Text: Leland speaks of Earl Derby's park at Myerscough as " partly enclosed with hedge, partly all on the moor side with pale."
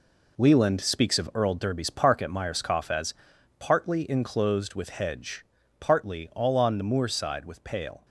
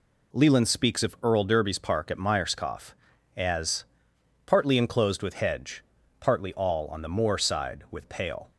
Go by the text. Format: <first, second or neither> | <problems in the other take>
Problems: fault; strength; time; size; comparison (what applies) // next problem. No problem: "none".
second | gets quieter; strong; throughout; 7.5 dB